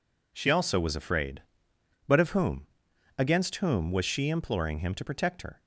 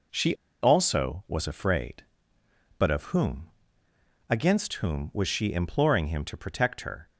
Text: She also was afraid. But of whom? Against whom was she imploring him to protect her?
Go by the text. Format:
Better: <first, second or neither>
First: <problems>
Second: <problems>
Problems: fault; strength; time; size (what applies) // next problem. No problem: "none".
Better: first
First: none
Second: pauses between "She" and "also"; slight; at 0.3 s; 0.27 s long